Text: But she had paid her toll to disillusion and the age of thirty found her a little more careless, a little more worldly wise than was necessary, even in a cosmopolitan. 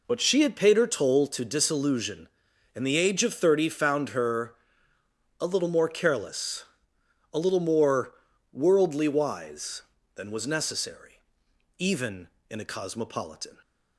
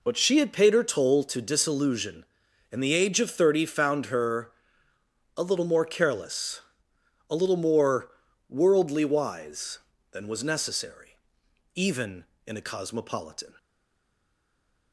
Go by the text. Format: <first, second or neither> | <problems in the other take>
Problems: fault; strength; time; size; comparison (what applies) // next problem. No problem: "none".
first | pauses between "her" and "a"; noticeable; at 4.5 s; 0.84 s long; noticeable in the first // pauses between "more" and "worldly"; at 8.0 s; 0.38 s long; also in the first // stays silent after the last word; noticeable; from 13.5 s on; 1.4 s long